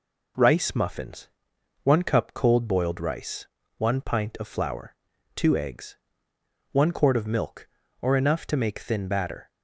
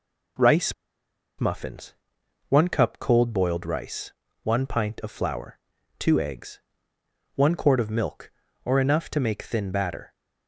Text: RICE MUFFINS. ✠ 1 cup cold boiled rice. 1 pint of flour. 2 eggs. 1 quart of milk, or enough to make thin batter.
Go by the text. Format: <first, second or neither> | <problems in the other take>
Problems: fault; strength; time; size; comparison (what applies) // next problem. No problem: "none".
first | pauses between "RICE" and "MUFFINS"; noticeable; at 0.7 s; 0.65 s long